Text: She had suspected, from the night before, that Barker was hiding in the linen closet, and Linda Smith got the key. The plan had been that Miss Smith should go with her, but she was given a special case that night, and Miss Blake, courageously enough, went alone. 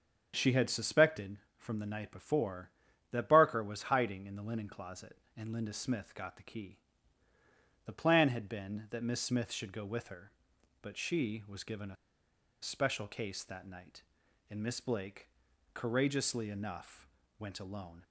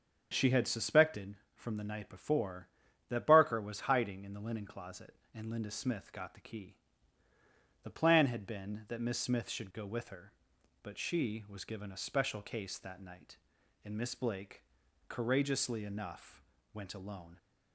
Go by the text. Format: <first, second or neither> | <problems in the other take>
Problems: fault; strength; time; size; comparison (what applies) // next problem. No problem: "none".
second | starts louder than the rest; strong; until 1.3 s; 7 dB; strong in the second // pauses between "a" and "special"; noticeable; at 11.9 s; 0.67 s long